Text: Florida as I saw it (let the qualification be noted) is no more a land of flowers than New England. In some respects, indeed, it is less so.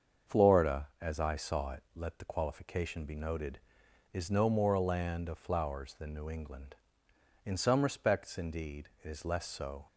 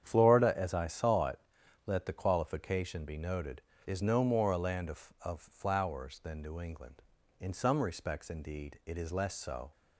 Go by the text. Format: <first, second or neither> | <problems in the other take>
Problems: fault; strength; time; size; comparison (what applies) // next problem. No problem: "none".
first | starts louder than the rest; strong; until 1.0 s; 8.5 dB; also in the first // says "of" twice; at 5.2 s